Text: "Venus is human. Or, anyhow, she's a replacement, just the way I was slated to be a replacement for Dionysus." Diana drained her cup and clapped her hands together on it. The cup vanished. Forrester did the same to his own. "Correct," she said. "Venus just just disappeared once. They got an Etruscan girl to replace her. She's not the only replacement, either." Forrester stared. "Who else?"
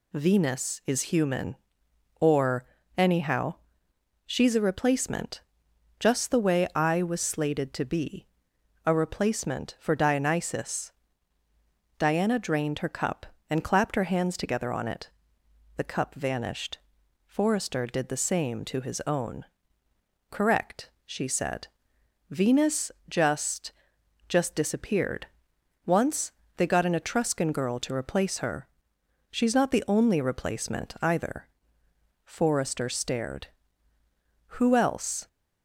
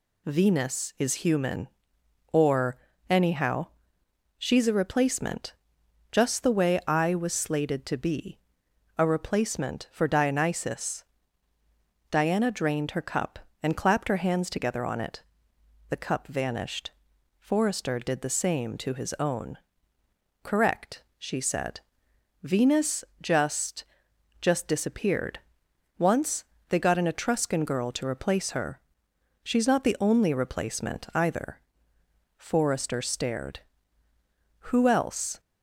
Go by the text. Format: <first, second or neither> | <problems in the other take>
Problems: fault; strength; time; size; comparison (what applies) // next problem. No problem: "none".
neither | pauses between "be" and "a"; noticeable; the same in both // pauses between "Venus" and "just"; slight; the same in both // pauses between "just" and "just"; noticeable; the same in both // pauses between "disappeared" and "once"; noticeable; the same in both